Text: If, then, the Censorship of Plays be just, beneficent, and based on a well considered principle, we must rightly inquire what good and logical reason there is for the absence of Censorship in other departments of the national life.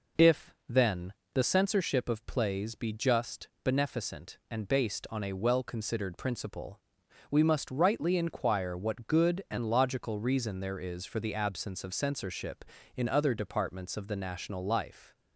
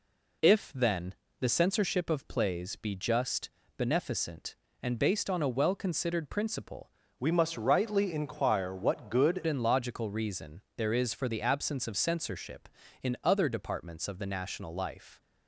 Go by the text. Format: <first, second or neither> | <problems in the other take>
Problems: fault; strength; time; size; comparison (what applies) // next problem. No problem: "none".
first | changes voice from "we" to "good"; from 7.1 to 9.4 s; 2.3 s long